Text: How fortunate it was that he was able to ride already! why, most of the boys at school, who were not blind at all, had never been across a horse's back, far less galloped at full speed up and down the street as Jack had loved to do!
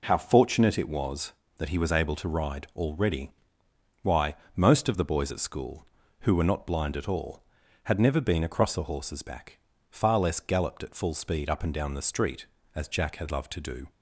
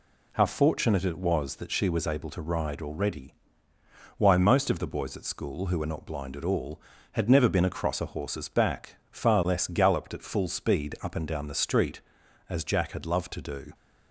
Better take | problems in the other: first | says "she" for "he"; at 1.7 s

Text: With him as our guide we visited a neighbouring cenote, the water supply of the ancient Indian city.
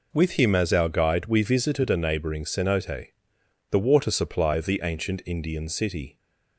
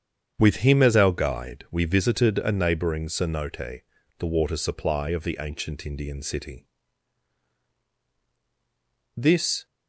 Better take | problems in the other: first | starts louder than the rest; strong; until 1.3 s; 8 dB // goes on to say "This"; slight; from 9.1 s on; 0.48 s long

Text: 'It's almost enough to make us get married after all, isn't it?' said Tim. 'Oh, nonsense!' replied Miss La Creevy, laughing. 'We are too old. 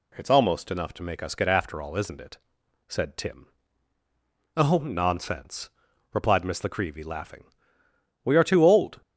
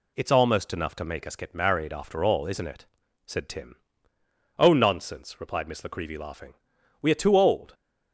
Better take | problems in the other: second | skips "married"; at 1.4 s

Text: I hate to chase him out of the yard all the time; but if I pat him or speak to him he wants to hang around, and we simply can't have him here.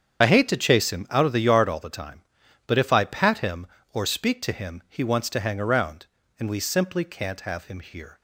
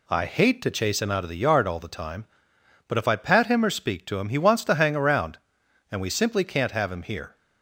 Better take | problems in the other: second | loses the start of "I"; at 0.2 s; 40 ms // starts louder than the rest; strong; until 1.2 s; 8 dB

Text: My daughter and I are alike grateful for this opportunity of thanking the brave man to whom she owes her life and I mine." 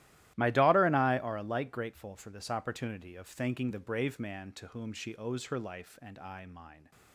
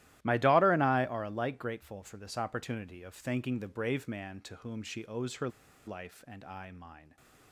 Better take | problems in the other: first | starts louder than the rest; strong; until 1.2 s; 15 dB; strong in the first // pauses between "her" and "life"; at 5.4 s; 0.38 s long // stays silent after the last word; slight; from 6.9 s on; 0.6 s long

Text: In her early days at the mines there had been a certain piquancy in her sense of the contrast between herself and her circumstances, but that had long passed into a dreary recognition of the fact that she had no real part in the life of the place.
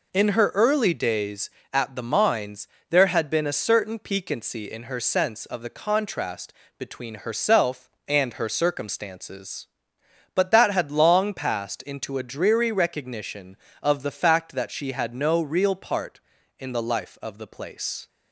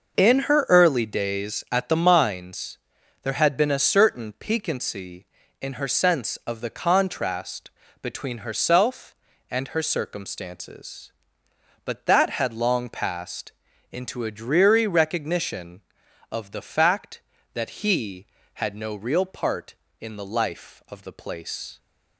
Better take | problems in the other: first | pauses between "mines" and "there"; at 2.7 s; 0.44 s long; slight in the first // pauses between "contrast" and "between"; slight; at 7.6 s; 0.30 s long; slight in the first // pauses between "passed" and "into"; at 13.5 s; 0.40 s long // says "he" for "she"; at 17.8 s

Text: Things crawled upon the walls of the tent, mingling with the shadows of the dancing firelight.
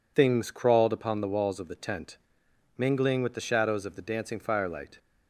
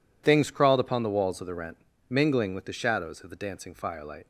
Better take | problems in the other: first | says "rent" for "tent"; at 1.5 s

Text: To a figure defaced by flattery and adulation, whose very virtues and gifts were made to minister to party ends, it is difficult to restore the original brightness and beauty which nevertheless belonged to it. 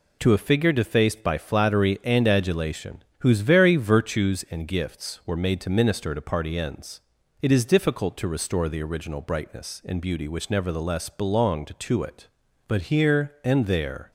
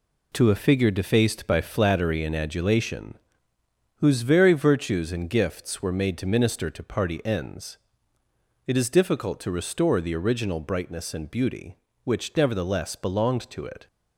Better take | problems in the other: second | goes on to say "But here and there"; from 12.6 s on; 1.4 s long

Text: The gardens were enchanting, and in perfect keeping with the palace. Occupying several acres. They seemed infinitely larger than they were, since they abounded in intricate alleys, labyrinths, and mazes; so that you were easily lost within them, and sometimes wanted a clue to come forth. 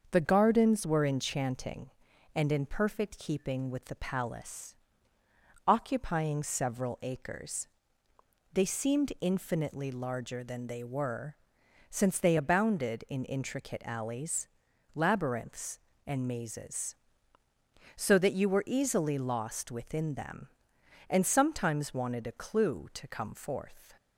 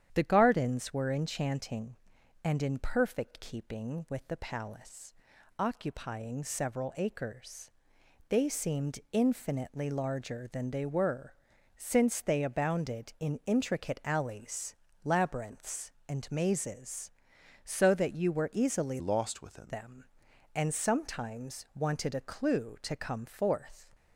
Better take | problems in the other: first | starts louder than the rest; strong; until 1.1 s; 9.5 dB; also in the first // changes voice from "lost" to "within"; from 18.9 to 19.7 s; 0.8 s long

